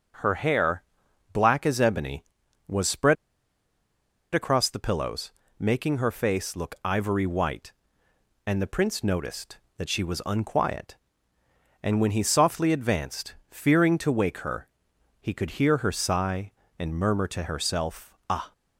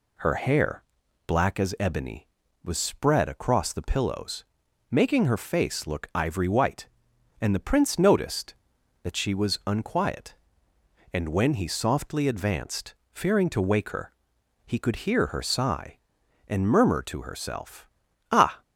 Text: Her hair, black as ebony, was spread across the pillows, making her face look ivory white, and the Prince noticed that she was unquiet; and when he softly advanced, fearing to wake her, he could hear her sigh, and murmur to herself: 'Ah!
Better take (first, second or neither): second